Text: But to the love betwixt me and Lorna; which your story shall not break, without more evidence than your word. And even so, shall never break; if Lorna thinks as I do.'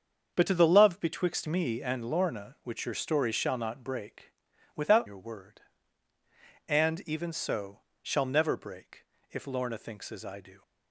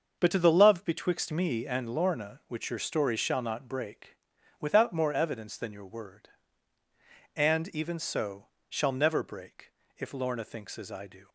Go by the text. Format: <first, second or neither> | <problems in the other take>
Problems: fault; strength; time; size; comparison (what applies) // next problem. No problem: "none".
second | starts louder than the rest; until 1.3 s; 7 dB; also in the second // skips "more evidence than"; at 5.0 s